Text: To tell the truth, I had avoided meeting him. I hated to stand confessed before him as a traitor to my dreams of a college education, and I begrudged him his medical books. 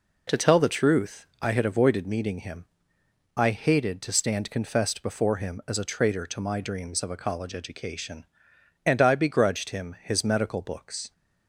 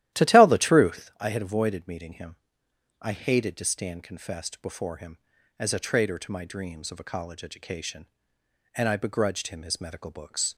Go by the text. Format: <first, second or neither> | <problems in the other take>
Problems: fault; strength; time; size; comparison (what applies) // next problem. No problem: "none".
first | starts louder than the rest; strong; until 1.1 s; 13.5 dB